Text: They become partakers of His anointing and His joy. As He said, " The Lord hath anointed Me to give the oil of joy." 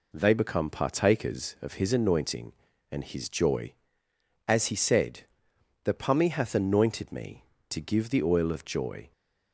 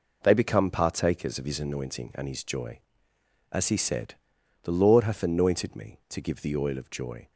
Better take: second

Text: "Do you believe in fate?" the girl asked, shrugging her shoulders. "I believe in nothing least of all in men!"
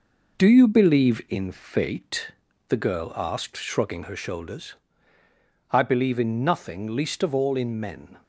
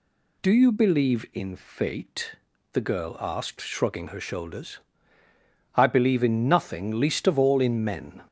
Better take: second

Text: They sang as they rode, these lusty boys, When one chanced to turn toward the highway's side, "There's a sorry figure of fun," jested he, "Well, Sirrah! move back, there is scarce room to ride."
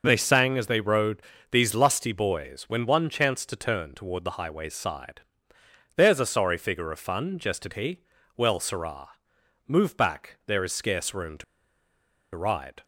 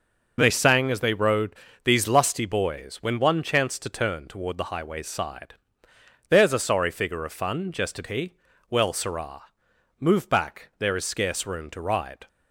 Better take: second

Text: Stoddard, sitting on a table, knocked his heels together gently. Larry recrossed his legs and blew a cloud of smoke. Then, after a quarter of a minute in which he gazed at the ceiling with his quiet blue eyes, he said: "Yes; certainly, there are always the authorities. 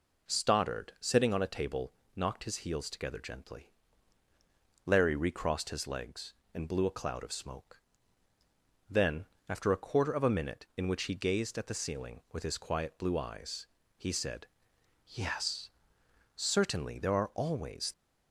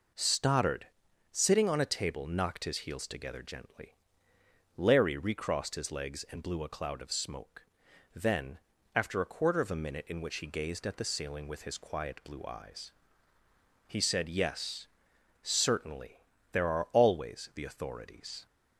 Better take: second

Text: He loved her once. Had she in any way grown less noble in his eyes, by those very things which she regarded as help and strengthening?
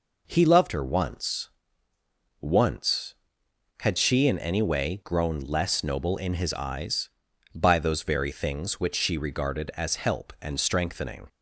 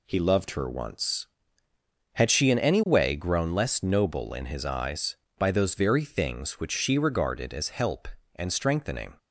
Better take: second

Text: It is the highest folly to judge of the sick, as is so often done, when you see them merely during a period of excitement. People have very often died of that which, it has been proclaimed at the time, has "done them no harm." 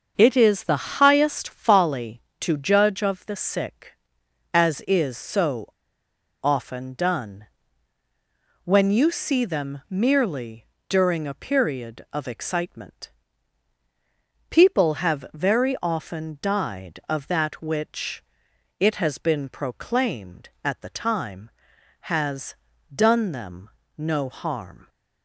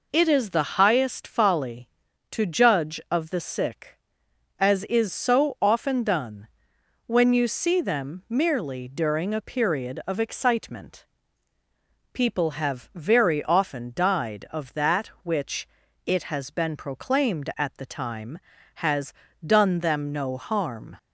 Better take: second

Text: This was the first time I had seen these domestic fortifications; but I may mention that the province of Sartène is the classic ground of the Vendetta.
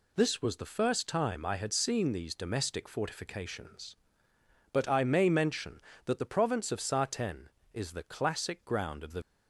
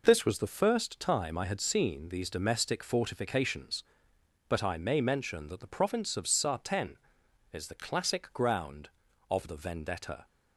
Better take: second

